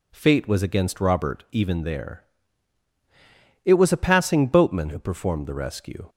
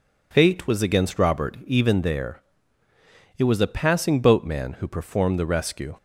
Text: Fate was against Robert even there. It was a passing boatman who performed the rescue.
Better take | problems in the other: neither | none

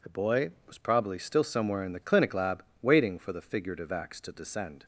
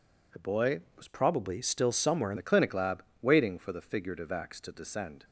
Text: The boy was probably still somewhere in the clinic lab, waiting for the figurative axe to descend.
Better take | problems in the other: first | changes voice from "probably" to "in"; from 1.0 to 2.3 s; 1.3 s long

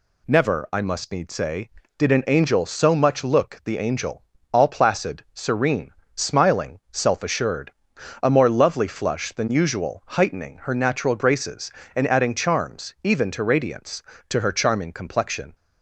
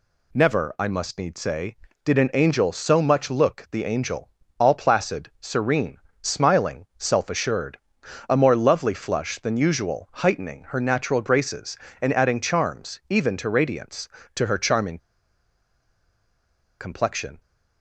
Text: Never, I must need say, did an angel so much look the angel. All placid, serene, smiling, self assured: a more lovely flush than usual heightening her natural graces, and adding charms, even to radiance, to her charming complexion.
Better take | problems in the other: first | pauses between "charming" and "complexion"; strong; at 14.9 s; 1.8 s long

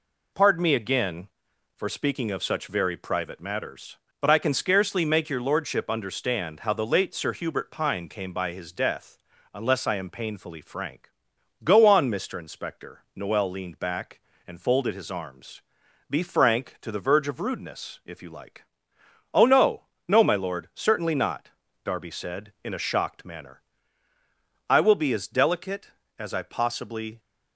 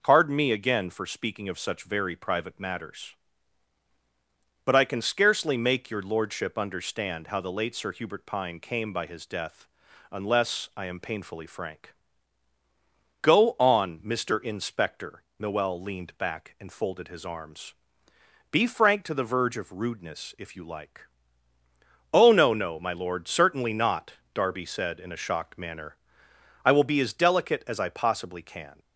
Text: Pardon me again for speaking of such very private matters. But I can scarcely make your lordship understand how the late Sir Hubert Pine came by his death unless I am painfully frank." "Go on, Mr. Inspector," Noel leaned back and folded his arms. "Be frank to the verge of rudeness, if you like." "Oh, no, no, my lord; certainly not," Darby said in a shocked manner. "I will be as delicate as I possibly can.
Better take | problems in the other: second | pauses between "death" and "unless"; slight; at 9.1 s; 0.36 s long; also in the second // stops before "can"; at 27.1 s

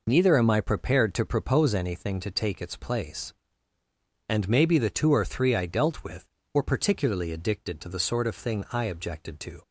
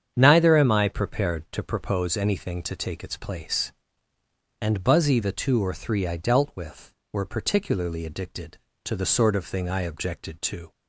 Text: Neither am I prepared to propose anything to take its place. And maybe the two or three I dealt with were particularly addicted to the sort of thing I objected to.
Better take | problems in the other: first | starts louder than the rest; strong; until 1.1 s; 8 dB // says "buzzy" for "maybe"; at 4.8 s

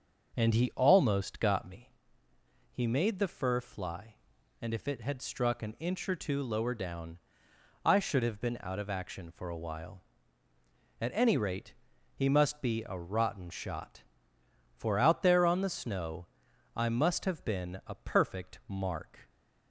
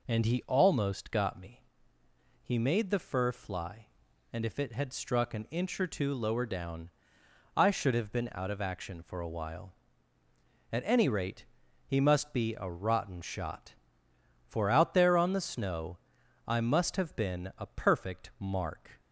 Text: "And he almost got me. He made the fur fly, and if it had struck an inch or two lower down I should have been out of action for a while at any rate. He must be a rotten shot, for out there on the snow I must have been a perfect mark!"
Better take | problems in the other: second | starts louder than the rest; noticeable; until 1.9 s; 6 dB // pauses between "down" and "I"; noticeable; at 7.1 s; 0.66 s long; noticeable in the second // pauses between "snow" and "I"; noticeable; at 16.2 s; 0.48 s long; noticeable in the second

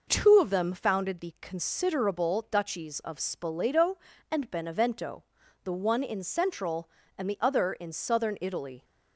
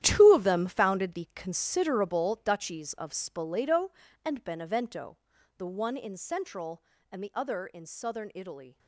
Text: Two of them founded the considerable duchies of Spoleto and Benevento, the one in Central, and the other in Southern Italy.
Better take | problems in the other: first | gets quieter; strong; throughout; 13.5 dB

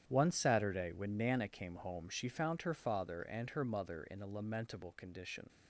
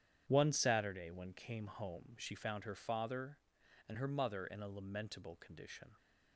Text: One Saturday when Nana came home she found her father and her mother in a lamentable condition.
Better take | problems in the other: first | starts louder than the rest; strong; until 1.2 s; 9.5 dB; strong in the first // skips "Nana"; at 1.3 s

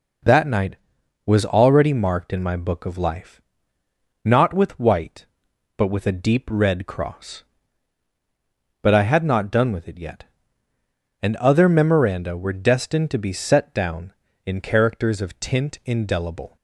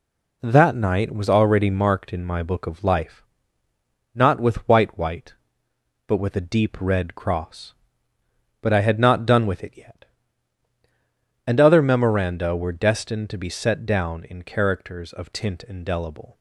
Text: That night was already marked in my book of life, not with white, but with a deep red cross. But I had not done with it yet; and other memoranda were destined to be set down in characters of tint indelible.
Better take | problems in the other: first | says "white" twice; at 4.9 s

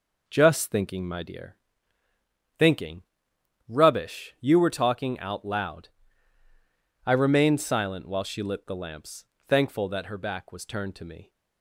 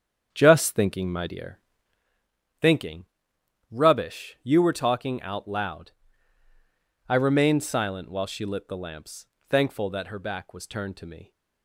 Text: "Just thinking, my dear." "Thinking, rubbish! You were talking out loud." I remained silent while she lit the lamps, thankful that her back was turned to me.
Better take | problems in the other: first | starts louder than the rest; strong; until 2.1 s; 8 dB

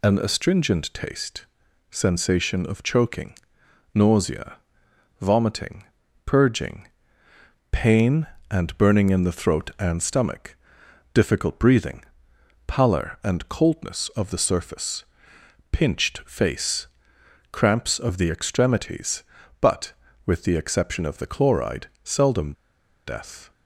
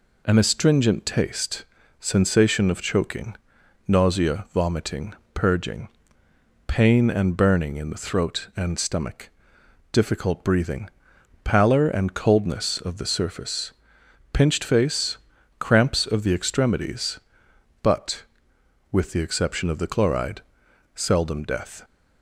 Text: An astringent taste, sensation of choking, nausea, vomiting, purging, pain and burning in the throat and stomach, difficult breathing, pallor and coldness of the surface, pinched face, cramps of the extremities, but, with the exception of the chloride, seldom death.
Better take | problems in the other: second | pauses between "seldom" and "death"; noticeable; at 22.5 s; 0.54 s long

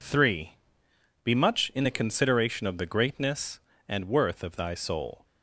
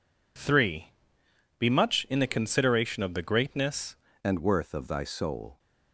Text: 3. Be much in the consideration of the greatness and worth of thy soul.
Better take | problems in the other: first | changes voice at "and"; from 4.2 s on; 1.3 s long

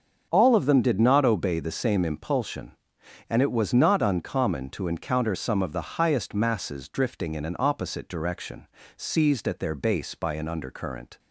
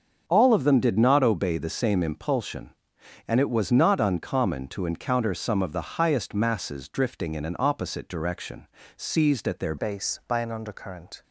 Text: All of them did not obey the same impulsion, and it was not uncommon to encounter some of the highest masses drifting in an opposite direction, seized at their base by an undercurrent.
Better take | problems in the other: first | starts louder than the rest; until 1.2 s; 7 dB; also in the first // changes voice at "base"; from 9.7 s on; 1.5 s long

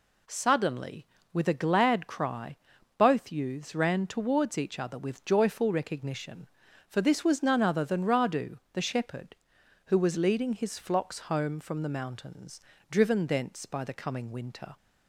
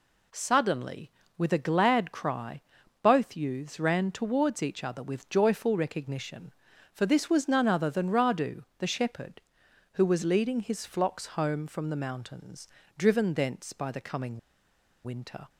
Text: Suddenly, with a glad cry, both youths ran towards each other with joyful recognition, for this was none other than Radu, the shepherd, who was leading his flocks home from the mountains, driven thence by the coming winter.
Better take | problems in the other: first | pauses between "coming" and "winter"; noticeable; at 14.3 s; 0.66 s long

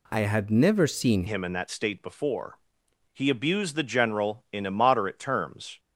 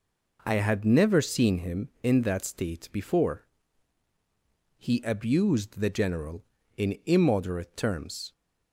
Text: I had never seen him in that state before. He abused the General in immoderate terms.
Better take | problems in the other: second | changes voice at "him"; from 1.2 s on; 4.5 s long

